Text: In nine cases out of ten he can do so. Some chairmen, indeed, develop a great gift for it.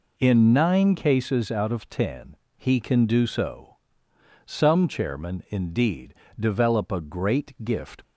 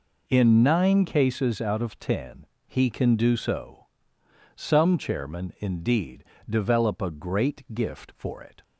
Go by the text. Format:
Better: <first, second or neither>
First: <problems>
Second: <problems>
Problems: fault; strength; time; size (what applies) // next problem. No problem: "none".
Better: second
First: pauses between "ten" and "he"; slight; at 2.3 s; 0.20 s long // stops before "for it"; at 8.0 s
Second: pauses between "ten" and "he"; slight; at 2.4 s; 0.20 s long